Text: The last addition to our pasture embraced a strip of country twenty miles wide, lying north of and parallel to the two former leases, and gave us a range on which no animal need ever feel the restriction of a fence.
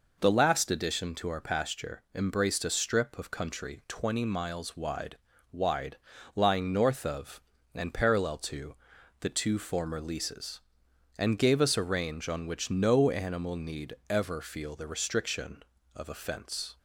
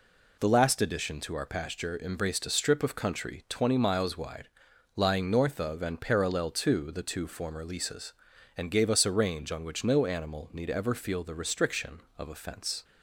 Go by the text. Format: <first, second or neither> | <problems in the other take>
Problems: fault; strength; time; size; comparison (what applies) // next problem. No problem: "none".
second | says "wide" twice; at 5.5 s // pauses between "to" and "the"; noticeable; at 8.7 s; 0.46 s long // pauses between "need" and "ever"; slight; at 13.9 s; 0.16 s long